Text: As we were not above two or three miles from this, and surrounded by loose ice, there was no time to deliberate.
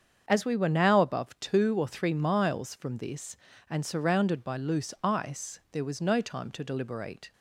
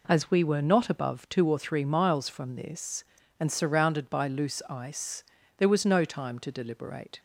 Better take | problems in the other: second | starts louder than the rest; strong; until 1.2 s; 7.5 dB // says "now" for "not"; at 0.6 s

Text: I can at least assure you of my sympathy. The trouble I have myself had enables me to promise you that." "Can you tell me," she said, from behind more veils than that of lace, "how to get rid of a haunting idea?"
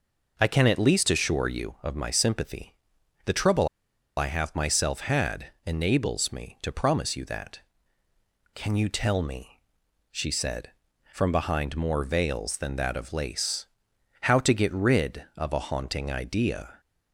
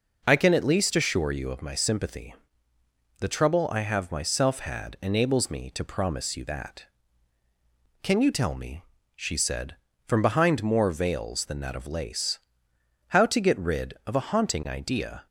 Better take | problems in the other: second | pauses between "trouble" and "I"; noticeable; at 3.6 s; 0.50 s long // pauses between "had" and "enables"; slight; at 5.4 s; 0.18 s long

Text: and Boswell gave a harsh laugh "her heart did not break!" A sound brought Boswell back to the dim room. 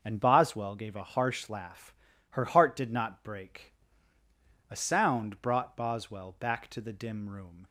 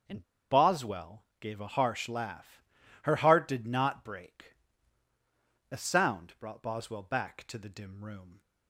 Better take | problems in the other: first | starts louder than the rest; strong; until 1.5 s; 7 dB; also in the first // pauses between "and" and "Boswell"; slight; at 0.2 s; 0.29 s long // pauses between "Boswell" and "gave"; slight; at 1.2 s; 0.16 s long // pauses between "laugh" and "her"; at 2.6 s; 0.40 s long; also in the first

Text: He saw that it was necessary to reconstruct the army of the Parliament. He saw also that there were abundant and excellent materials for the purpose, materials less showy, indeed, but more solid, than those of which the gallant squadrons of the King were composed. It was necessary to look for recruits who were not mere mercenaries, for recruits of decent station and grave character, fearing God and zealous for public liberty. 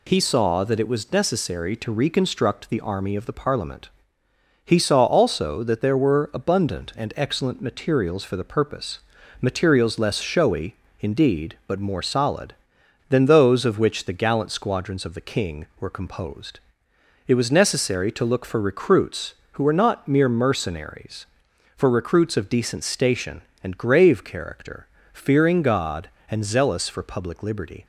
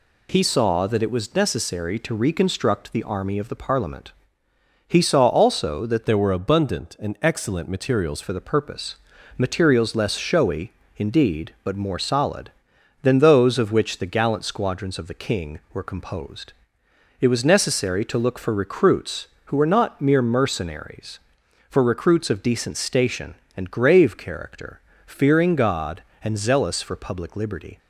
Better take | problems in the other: first | changes voice from "there" to "materials"; from 6.0 to 8.2 s; 2.2 s long

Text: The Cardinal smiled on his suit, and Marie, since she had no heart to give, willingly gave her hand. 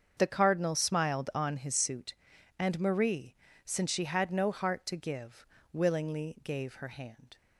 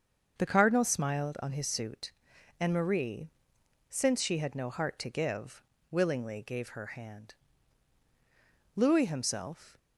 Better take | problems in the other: first | starts louder than the rest; until 1.3 s; 7 dB; also in the first // goes on to say "Louis himself"; noticeable; from 8.7 s on; 1.0 s long

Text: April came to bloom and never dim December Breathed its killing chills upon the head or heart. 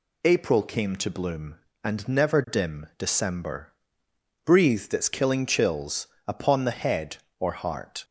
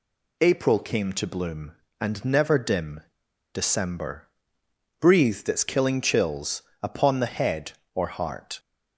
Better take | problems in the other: first | pauses between "dim" and "December"; noticeable; at 3.0 s; 0.53 s long // pauses between "December" and "Breathed"; noticeable; at 4.2 s; 0.72 s long; noticeable in the first // pauses between "chills" and "upon"; slight; at 6.6 s; 0.20 s long; slight in the first

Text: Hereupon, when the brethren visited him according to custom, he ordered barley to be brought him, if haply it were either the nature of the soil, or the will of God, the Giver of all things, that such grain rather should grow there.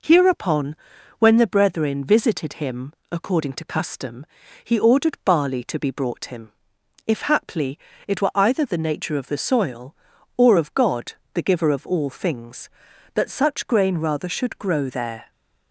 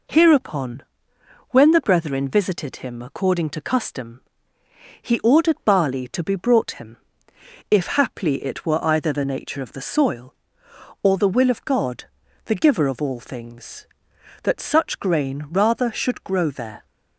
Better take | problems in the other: second | pauses between "him" and "according"; slight; at 2.9 s; 0.18 s long // pauses between "haply" and "it"; slight; at 7.7 s; 0.30 s long // skips "the will"; at 10.5 s

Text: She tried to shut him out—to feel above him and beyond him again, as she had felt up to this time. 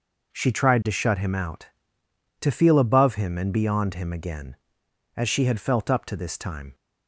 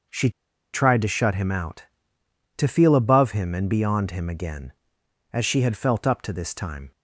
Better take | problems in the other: first | pauses between "She" and "tried"; at 0.2 s; 0.43 s long

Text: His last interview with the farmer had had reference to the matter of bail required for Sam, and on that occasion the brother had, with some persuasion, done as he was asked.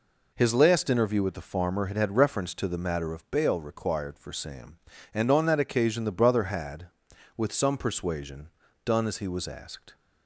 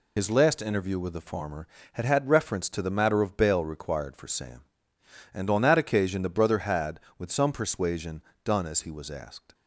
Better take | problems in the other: first | loses the start of "His"; at 0.1 s; 50 ms

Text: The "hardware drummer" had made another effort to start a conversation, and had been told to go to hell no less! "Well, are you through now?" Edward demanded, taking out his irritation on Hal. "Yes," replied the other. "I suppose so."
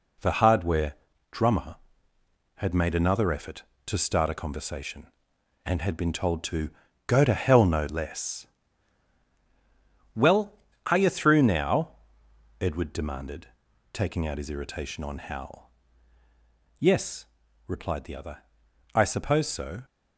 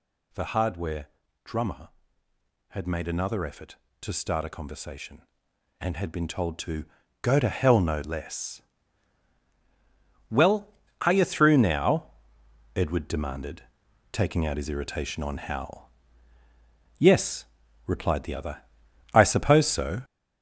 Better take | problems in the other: first | gets louder; noticeable; throughout; 6 dB // pauses between "hardware" and "drummer"; slight; at 1.0 s; 0.36 s long; slight in the first // pauses between "to" and "go"; slight; at 6.8 s; 0.34 s long; slight in the first

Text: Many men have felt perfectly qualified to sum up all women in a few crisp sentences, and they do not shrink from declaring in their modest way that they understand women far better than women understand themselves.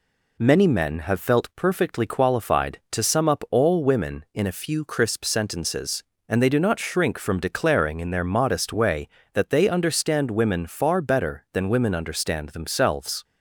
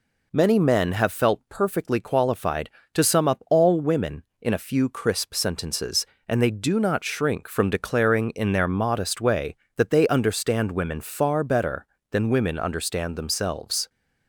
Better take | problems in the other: neither | none

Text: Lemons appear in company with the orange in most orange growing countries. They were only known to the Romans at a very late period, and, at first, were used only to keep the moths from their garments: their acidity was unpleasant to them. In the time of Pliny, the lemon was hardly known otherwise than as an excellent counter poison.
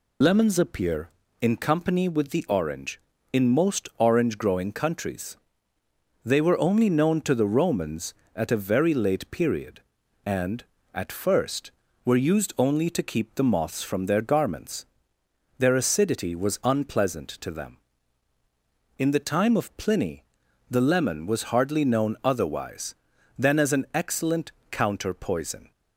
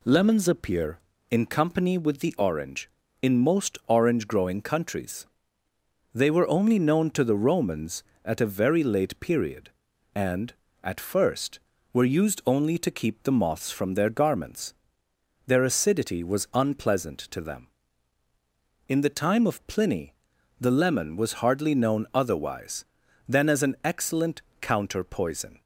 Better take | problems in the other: second | loses the start of "Lemons"; at 0.2 s; 75 ms // pauses between "excellent" and "counter"; slight; at 24.5 s; 0.20 s long; slight in the second

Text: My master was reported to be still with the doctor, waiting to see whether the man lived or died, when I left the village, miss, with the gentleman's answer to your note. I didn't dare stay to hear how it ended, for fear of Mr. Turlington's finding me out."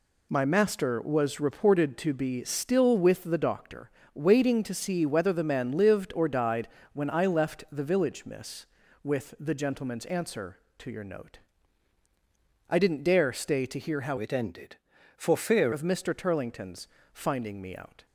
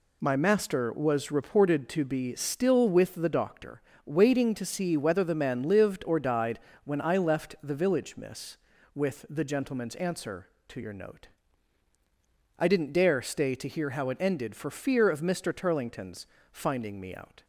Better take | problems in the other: second | changes voice from "it" to "fear"; from 14.1 to 15.7 s; 1.6 s long // pauses between "Turlington's" and "finding"; slight; at 16.8 s; 0.26 s long; slight in the second

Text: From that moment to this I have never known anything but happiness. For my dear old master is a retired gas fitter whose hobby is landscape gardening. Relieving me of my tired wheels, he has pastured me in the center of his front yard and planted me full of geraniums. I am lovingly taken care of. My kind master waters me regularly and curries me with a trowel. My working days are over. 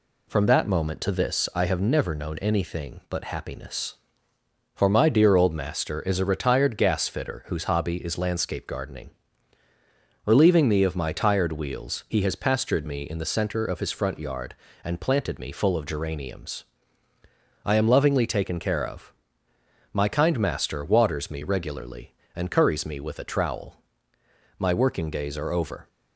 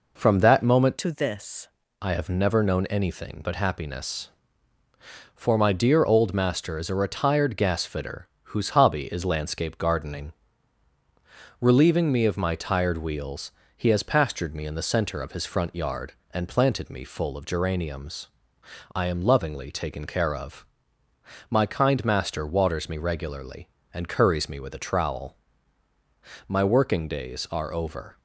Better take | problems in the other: first | changes voice from "to" to "this"; from 0.9 to 1.6 s; 0.7 s long // pauses between "fitter" and "whose"; slight; at 8.2 s; 0.16 s long

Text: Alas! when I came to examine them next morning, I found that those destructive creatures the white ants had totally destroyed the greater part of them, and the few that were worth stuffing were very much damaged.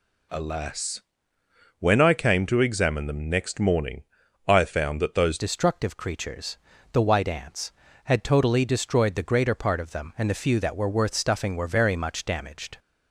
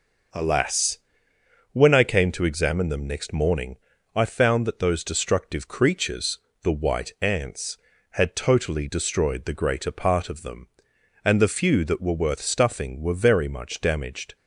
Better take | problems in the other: second | changes voice at "destructive"; from 5.3 s on; 7.4 s long // pauses between "creatures" and "the"; slight; at 6.5 s; 0.36 s long; slight in the second

